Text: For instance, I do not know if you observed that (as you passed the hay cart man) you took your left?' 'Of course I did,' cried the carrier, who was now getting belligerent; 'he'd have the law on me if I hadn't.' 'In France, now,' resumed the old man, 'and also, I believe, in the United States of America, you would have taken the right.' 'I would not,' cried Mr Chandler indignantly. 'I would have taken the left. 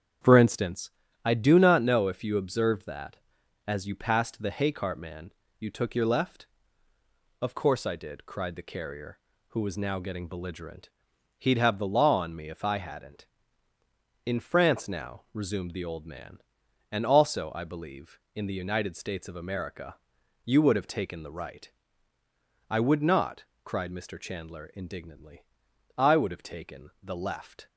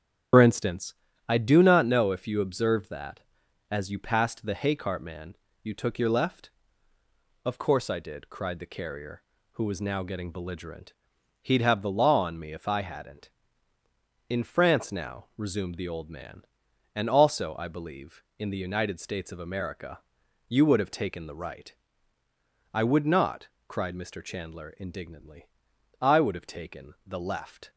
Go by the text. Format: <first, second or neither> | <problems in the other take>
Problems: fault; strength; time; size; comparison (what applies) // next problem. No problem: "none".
first | loses the start of "For"; at 0.3 s; 75 ms // starts louder than the rest; strong; until 1.6 s; 9 dB; strong in the first